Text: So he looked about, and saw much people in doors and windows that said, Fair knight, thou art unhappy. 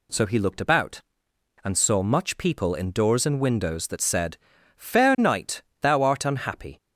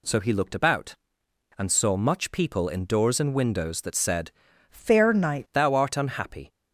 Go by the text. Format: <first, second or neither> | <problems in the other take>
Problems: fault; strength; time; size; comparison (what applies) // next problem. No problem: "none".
first | changes voice from "Fair" to "knight"; from 4.6 to 5.4 s; 0.8 s long